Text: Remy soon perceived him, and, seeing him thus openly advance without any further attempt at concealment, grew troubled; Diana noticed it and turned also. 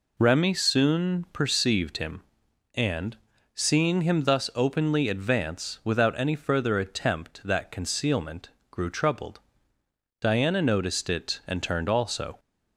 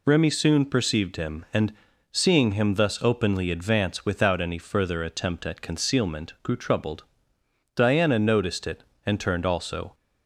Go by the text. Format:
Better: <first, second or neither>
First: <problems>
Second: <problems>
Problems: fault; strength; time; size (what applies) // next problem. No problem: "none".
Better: second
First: says "that" for "at"; at 7.4 s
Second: none